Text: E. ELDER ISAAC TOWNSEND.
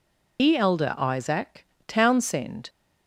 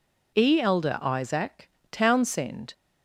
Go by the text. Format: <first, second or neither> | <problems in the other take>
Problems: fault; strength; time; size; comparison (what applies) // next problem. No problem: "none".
second | loses the start of "E"; at 0.3 s; 90 ms // pauses between "ISAAC" and "TOWNSEND"; slight; at 1.6 s; 0.22 s long; slight in the second